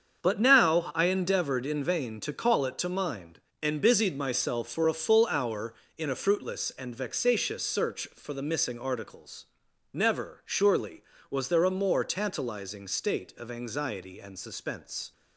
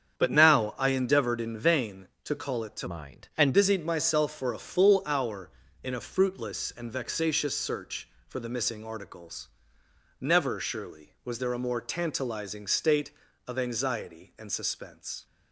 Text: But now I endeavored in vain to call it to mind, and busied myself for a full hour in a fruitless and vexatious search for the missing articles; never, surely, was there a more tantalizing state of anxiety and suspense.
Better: first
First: starts louder than the rest; strong; until 1.2 s; 7 dB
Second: starts louder than the rest; strong; until 1.2 s; 8 dB // changes voice from "mind" to "and"; from 2.8 to 3.5 s; 0.7 s long

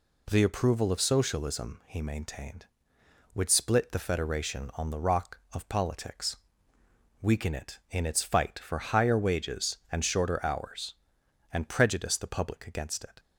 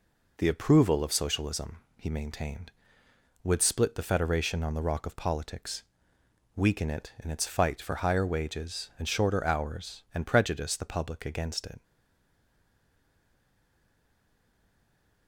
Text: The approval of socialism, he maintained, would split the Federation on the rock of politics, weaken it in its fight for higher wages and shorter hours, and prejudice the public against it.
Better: first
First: none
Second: stays silent after the last word; strong; from 11.8 s on; 3.4 s long

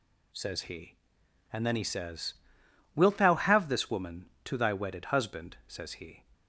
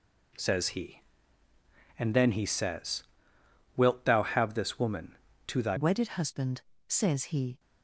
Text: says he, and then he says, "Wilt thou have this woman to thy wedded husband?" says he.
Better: first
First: none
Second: changes voice at "wedded"; from 5.7 s on; 1.8 s long

